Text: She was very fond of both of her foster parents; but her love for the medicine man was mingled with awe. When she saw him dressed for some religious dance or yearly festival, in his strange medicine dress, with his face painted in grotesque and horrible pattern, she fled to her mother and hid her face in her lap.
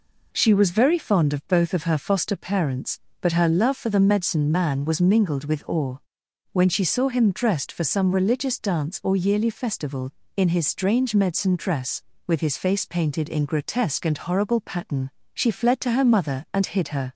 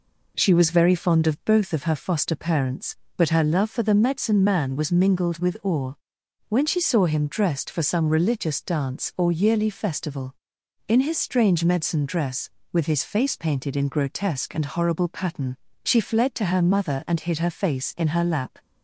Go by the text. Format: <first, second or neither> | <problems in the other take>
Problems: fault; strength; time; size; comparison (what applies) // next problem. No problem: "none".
second | stops before "face in her lap"; at 17.1 s